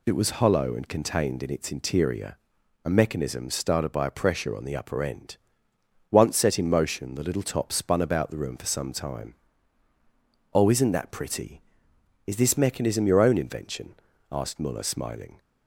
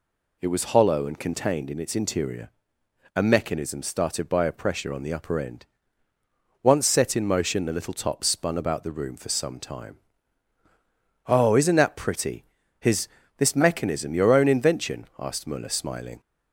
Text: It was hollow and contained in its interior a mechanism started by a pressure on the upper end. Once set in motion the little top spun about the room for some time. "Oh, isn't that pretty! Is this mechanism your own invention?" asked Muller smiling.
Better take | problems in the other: first | pauses between "interior" and "a"; noticeable; at 2.5 s; 0.66 s long; noticeable in the first // says "His" for "Is"; at 12.7 s

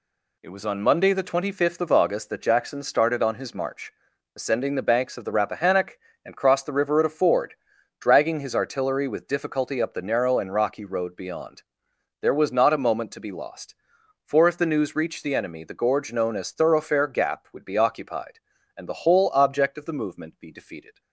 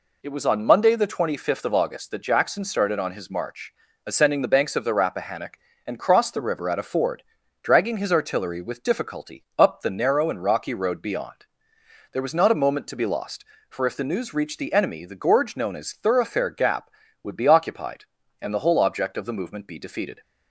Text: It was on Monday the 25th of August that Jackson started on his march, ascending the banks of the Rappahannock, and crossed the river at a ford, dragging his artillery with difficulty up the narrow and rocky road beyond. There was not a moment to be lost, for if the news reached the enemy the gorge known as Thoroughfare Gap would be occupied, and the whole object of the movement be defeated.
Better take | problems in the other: neither | none

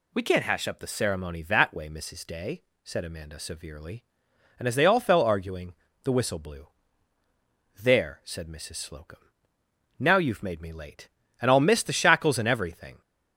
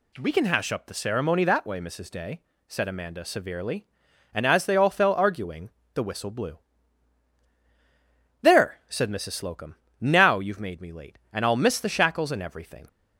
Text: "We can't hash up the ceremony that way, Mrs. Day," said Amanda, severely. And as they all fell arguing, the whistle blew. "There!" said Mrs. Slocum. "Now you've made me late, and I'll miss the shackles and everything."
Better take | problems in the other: first | says "can" for "can't"; at 0.3 s

